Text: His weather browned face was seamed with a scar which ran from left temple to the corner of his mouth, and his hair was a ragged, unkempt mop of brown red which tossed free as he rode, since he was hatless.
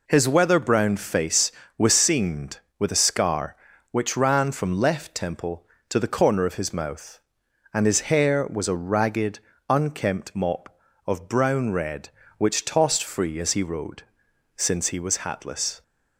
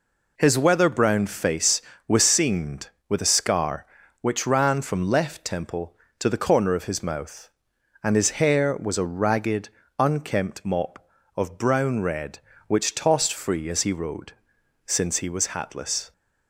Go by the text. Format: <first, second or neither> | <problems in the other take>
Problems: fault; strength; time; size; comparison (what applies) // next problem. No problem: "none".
neither | none